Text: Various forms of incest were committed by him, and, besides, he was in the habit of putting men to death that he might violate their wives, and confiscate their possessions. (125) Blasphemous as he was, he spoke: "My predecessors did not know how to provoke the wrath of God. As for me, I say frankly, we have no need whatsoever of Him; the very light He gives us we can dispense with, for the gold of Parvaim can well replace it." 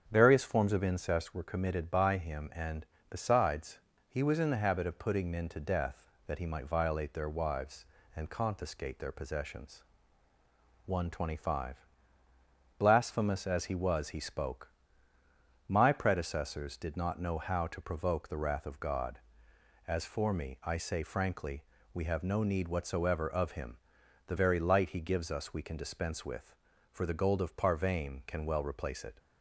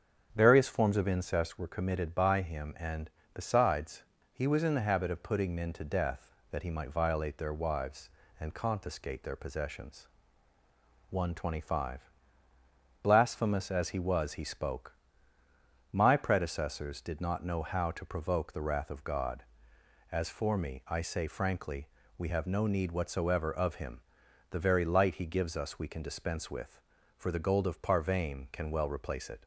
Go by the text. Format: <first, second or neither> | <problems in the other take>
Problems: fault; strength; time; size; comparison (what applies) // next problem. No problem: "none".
neither | starts louder than the rest; strong; the same in both